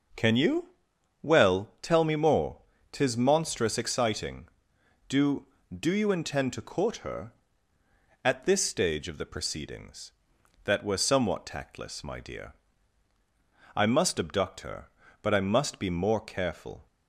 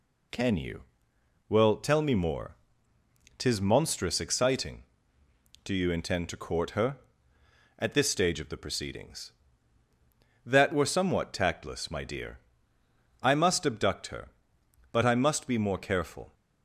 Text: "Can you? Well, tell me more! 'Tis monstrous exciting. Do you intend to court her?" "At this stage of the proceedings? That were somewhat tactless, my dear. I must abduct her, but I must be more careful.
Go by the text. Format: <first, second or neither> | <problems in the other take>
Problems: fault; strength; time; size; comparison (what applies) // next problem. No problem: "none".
second | says "Do" twice; at 5.7 s